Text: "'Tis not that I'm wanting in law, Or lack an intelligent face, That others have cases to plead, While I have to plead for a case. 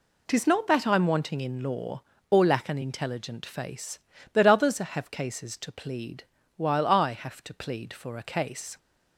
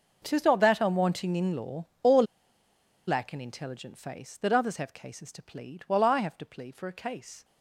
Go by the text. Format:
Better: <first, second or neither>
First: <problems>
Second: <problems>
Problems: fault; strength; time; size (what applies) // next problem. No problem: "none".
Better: first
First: none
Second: starts louder than the rest; noticeable; until 1.2 s; 6 dB // pauses between "Or" and "lack"; noticeable; at 2.2 s; 0.84 s long